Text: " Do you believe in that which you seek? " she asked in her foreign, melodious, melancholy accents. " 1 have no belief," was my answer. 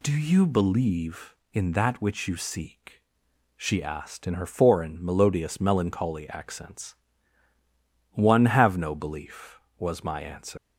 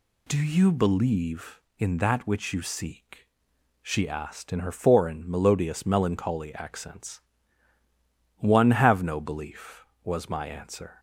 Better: second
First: leaves "answer" unfinished; at 10.5 s; 165 ms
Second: none

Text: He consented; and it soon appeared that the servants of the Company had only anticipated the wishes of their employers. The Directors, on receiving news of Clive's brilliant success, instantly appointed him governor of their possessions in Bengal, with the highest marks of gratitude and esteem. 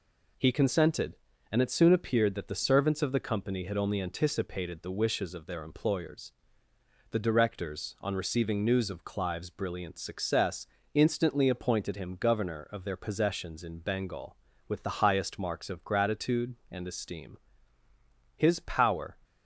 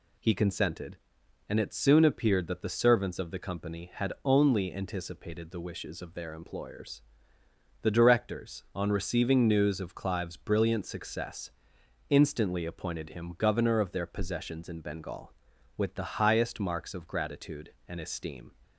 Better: second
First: goes on to say "His power"; noticeable; from 18.3 s on; 0.80 s long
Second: none

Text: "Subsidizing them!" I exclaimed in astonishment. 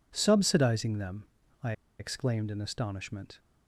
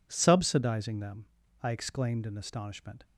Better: second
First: pauses between "I" and "exclaimed"; slight; at 1.7 s; 0.27 s long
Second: none

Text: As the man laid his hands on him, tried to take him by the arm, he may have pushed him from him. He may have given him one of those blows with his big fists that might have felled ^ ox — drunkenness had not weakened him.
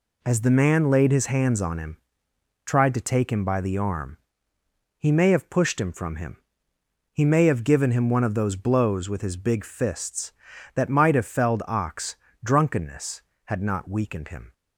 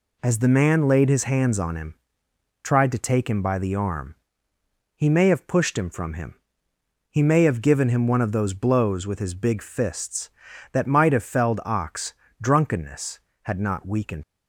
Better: first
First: none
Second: stops before "him"; at 14.2 s

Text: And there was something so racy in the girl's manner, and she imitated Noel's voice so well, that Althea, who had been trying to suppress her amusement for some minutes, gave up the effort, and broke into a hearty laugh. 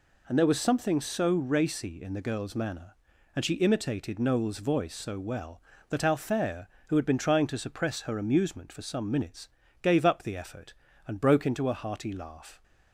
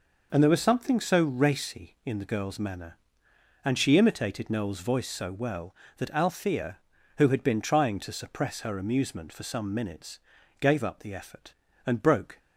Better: first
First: none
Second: stops before "into a hearty laugh"; at 12.3 s

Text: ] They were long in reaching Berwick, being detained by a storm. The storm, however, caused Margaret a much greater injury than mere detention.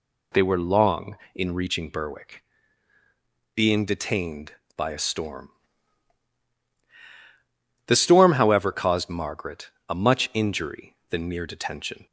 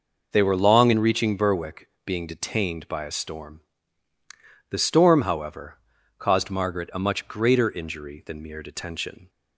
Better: second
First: pauses between "Margaret" and "a"; slight; at 9.6 s; 0.20 s long // skips "greater"; at 10.3 s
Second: none

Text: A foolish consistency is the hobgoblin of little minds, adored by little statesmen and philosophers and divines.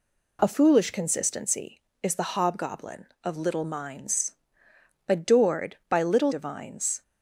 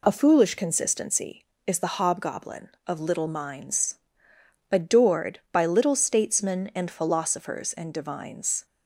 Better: second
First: skips "statesmen and philosophers and"; at 6.3 s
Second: none

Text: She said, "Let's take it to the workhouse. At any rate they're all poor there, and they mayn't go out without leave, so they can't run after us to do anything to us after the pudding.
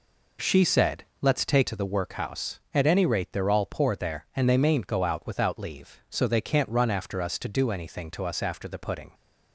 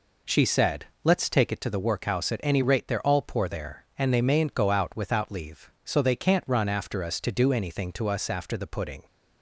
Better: second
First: skips "it"; at 1.6 s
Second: none

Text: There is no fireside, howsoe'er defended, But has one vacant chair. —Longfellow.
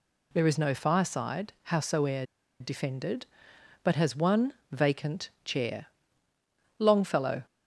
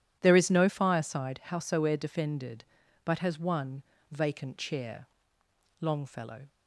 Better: second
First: pauses between "howsoe'er" and "defended"; slight; at 2.2 s; 0.35 s long // pauses between "one" and "vacant"; slight; at 4.5 s; 0.20 s long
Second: pauses between "one" and "vacant"; slight; at 3.8 s; 0.28 s long

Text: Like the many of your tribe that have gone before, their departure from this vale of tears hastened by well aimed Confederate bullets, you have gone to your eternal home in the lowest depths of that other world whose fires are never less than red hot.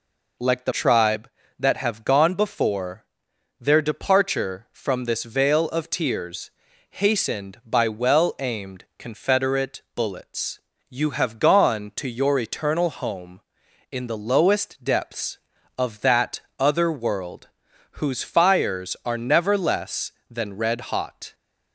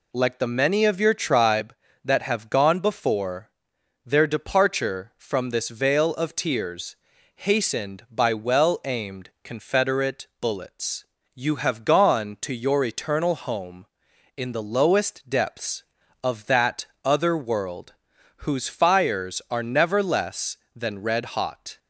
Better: second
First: skips "many of your"; at 0.7 s // pauses between "tears" and "hastened"; at 6.4 s; 0.40 s long // pauses between "that" and "other"; slight; at 16.3 s; 0.18 s long // pauses between "world" and "whose"; noticeable; at 17.4 s; 0.48 s long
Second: pauses between "tears" and "hastened"; at 6.9 s; 0.40 s long // pauses between "that" and "other"; slight; at 16.8 s; 0.18 s long // pauses between "world" and "whose"; noticeable; at 17.9 s; 0.48 s long

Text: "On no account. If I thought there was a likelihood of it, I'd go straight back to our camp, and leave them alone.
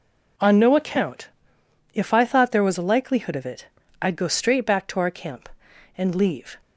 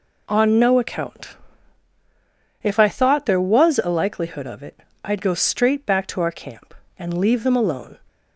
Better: second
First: stops before "them alone"; at 6.6 s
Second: none

